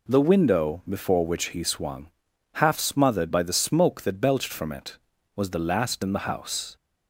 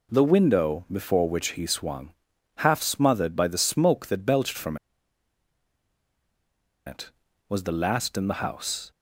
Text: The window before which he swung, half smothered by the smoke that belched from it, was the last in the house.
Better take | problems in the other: first | pauses between "from" and "it"; strong; at 4.7 s; 2.1 s long

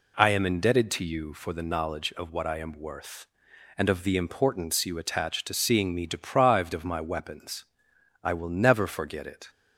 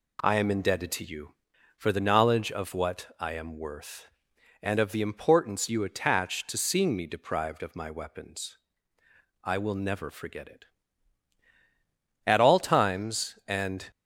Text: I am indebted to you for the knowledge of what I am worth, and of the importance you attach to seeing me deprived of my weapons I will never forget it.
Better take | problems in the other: first | pauses between "weapons" and "I"; noticeable; at 8.5 s; 0.86 s long; noticeable in the first // goes on to say "At all times and"; strong; from 12.2 s on; 1.6 s long

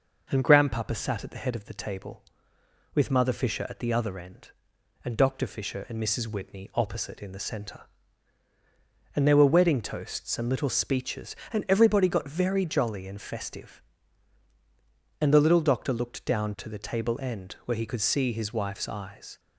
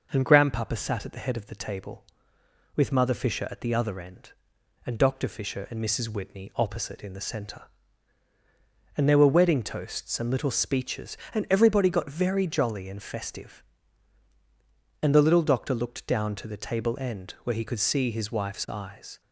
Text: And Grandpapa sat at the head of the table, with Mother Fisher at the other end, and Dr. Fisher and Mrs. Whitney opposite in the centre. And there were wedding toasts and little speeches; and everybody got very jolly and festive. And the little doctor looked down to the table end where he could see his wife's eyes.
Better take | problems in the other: neither | none

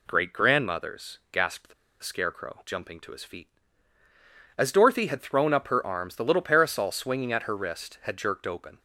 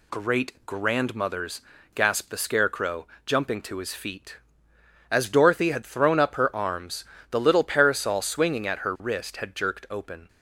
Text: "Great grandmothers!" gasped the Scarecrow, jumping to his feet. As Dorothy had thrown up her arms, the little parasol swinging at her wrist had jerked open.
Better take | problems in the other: second | pauses between "the" and "Scarecrow"; slight; at 1.7 s; 0.29 s long

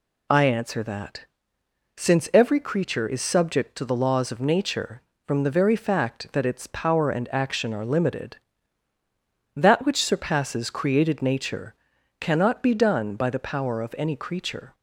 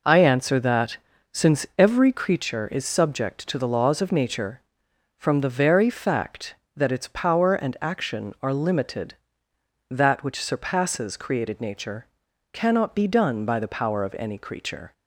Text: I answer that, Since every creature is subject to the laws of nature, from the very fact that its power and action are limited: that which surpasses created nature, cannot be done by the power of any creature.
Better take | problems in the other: neither | none

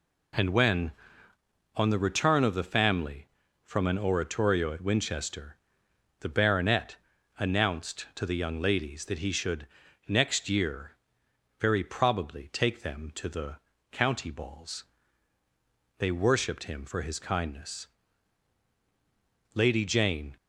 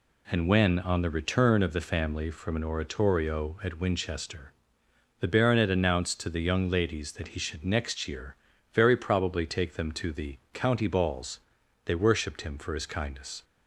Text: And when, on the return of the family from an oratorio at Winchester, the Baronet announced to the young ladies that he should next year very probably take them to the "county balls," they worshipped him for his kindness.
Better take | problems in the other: second | pauses between "Baronet" and "announced"; at 6.9 s; 0.42 s long // pauses between "should" and "next"; at 9.6 s; 0.42 s long // pauses between "year" and "very"; noticeable; at 10.9 s; 0.68 s long; also in the second // pauses between "the" and "county"; slight; at 13.5 s; 0.34 s long // goes on to say "Lady Jane"; noticeable; from 19.5 s on; 0.82 s long

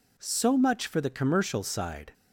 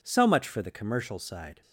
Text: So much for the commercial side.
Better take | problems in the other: neither | none

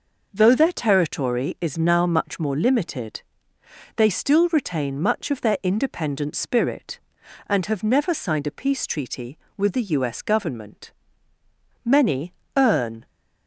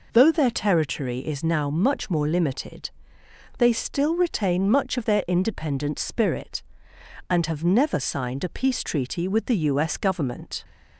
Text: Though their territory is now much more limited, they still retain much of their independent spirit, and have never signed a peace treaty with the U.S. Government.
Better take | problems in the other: second | goes on to say "Many earn"; noticeable; from 11.8 s on; 1.2 s long

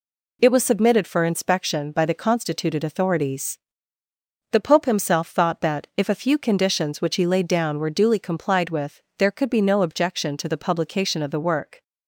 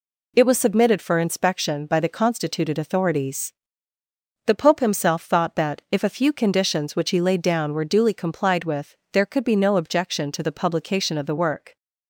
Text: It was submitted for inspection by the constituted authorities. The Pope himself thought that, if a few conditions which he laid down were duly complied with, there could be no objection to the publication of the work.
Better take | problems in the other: neither | none

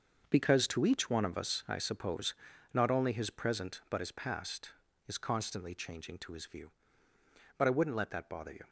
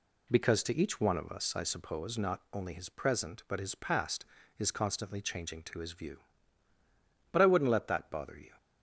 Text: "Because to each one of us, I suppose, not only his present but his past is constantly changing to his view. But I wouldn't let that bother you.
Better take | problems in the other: second | gets quieter; strong; throughout; 11 dB

